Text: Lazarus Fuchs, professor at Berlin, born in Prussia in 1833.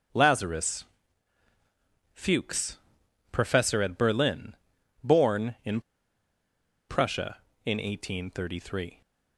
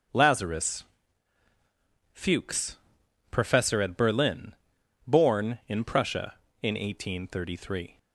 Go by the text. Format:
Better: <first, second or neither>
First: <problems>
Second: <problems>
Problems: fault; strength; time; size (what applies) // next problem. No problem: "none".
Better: second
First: starts louder than the rest; strong; until 2.3 s; 7.5 dB // pauses between "Lazarus" and "Fuchs"; strong; at 0.8 s; 1.2 s long // pauses between "in" and "Prussia"; at 5.8 s; 1.0 s long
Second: starts louder than the rest; strong; until 2.4 s; 7.5 dB // pauses between "Lazarus" and "Fuchs"; strong; at 0.8 s; 1.2 s long